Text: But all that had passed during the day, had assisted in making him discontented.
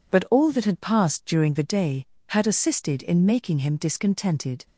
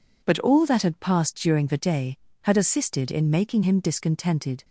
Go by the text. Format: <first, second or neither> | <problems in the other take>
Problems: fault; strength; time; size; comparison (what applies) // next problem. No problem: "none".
neither | none